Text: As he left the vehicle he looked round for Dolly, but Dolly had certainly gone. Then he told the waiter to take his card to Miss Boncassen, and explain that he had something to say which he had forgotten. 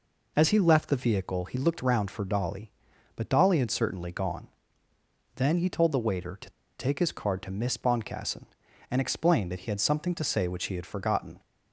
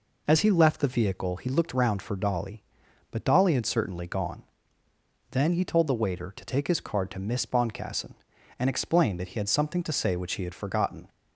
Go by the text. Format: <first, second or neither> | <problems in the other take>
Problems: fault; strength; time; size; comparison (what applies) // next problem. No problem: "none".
second | pauses between "to" and "take"; slight; at 6.4 s; 0.29 s long